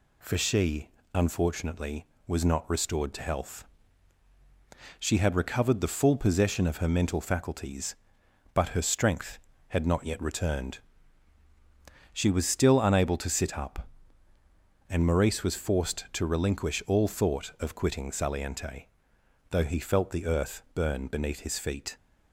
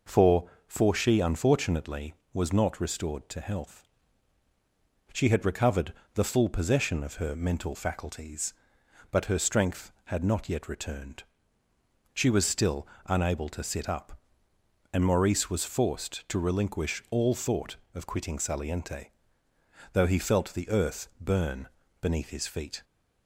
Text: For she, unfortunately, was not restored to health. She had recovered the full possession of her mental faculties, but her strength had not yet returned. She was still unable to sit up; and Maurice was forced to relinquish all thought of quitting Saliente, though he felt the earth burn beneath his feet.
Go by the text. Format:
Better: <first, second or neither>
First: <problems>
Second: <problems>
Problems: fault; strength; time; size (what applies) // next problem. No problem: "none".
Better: first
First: none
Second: says "For" twice; at 0.6 s // pauses between "recovered" and "the"; slight; at 5.9 s; 0.22 s long // pauses between "still" and "unable"; slight; at 12.8 s; 0.22 s long // pauses between "burn" and "beneath"; slight; at 21.6 s; 0.32 s long